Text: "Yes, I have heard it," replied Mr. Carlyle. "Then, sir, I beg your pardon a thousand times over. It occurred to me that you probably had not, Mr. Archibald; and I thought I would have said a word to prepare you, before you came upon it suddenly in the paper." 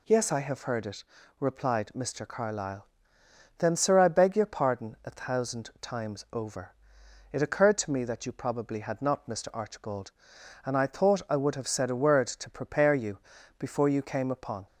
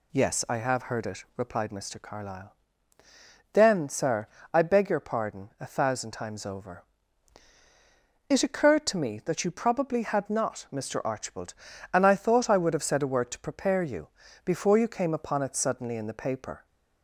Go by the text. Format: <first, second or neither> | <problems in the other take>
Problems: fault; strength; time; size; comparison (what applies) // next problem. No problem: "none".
second | stops before "it suddenly in the paper"; at 14.6 s